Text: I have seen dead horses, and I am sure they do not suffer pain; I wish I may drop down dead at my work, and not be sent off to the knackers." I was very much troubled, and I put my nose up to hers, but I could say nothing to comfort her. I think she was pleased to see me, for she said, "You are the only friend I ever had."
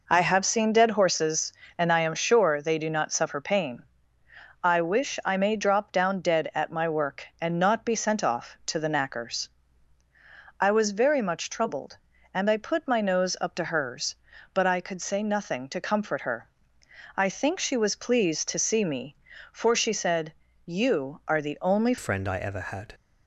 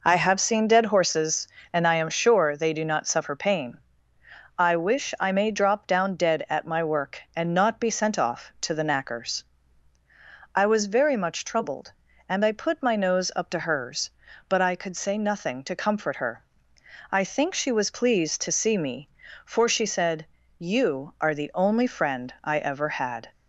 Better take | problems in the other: second | changes voice at "friend"; from 21.9 s on; 1.0 s long

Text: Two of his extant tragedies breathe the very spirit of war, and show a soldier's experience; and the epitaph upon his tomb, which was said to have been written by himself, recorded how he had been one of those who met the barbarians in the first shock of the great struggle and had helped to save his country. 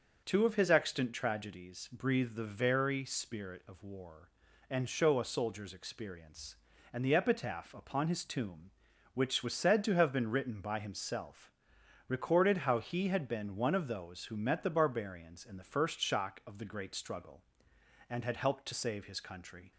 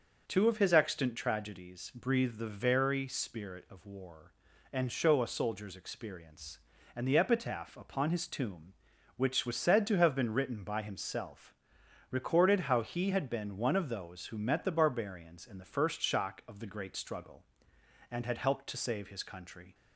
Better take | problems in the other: neither | starts louder than the rest; noticeable; the same in both

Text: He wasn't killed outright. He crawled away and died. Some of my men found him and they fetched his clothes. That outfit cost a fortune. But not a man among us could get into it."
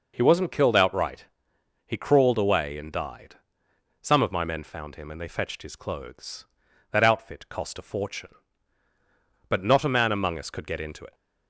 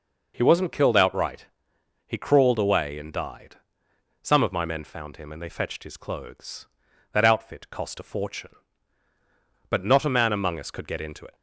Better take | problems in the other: neither | none

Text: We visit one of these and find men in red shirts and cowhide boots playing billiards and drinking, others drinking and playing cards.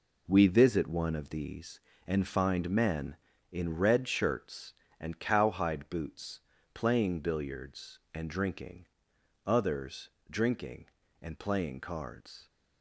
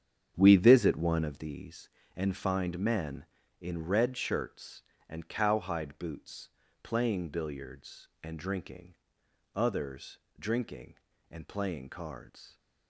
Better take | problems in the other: first | starts louder than the rest; strong; until 1.5 s; 8.5 dB // pauses between "boots" and "playing"; slight; at 6.4 s; 0.34 s long; slight in the first // pauses between "others" and "drinking"; slight; at 10.1 s; 0.22 s long; slight in the first

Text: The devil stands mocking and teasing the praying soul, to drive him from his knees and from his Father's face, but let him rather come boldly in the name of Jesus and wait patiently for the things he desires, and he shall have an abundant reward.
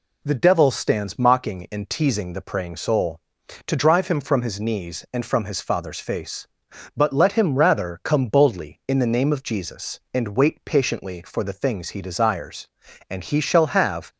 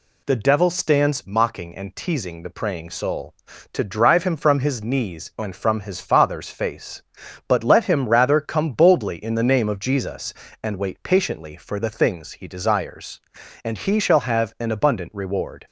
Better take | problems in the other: second | stops before "an abundant reward"; at 14.1 s

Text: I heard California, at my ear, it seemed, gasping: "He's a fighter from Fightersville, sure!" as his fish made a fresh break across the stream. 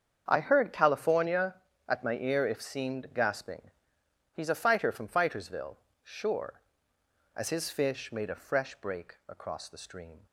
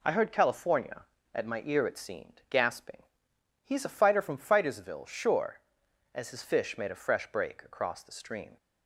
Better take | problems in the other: second | starts louder than the rest; strong; until 1.2 s; 7.5 dB // says "if" for "it"; at 2.4 s

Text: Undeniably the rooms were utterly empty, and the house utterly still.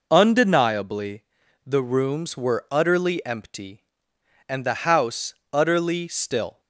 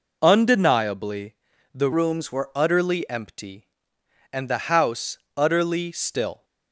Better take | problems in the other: first | pauses between "Undeniably" and "the"; at 1.3 s; 0.40 s long; also in the first // changes voice from "rooms" to "were"; from 1.9 to 2.5 s; 0.6 s long // pauses between "house" and "utterly"; slight; at 5.1 s; 0.18 s long; slight in the first

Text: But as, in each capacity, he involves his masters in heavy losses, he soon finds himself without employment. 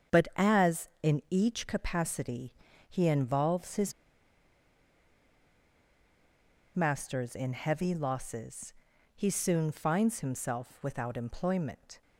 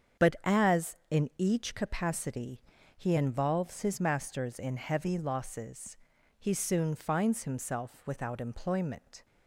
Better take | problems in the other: second | starts louder than the rest; strong; until 1.4 s; 7.5 dB; strong in the second // pauses between "his" and "masters"; strong; at 3.9 s; 2.8 s long

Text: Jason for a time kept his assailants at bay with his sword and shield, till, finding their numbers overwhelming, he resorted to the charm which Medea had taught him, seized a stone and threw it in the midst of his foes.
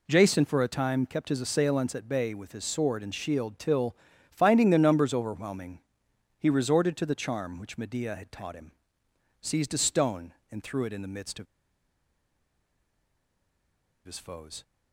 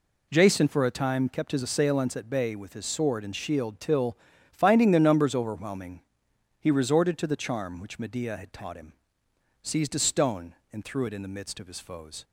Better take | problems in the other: second | pauses between "of" and "his"; strong; at 11.4 s; 2.5 s long

